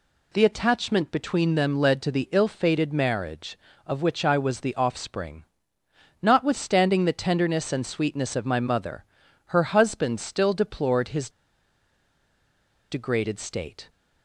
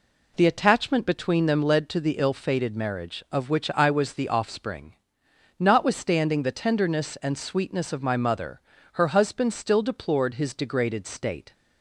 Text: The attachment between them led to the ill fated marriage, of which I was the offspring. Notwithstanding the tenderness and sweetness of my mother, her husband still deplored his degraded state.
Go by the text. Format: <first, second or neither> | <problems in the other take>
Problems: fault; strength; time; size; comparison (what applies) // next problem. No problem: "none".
second | pauses between "his" and "degraded"; strong; at 11.2 s; 1.6 s long